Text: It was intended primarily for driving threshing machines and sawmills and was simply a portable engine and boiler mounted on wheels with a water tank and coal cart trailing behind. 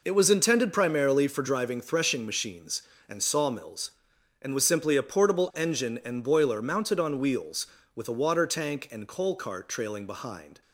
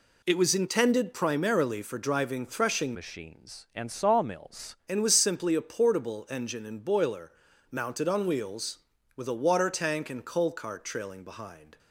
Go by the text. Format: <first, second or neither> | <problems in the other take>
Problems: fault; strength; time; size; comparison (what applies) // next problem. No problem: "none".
first | changes voice from "machines" to "sawmills"; from 2.9 to 4.7 s; 1.8 s long // pauses between "boiler" and "mounted"; at 7.3 s; 0.40 s long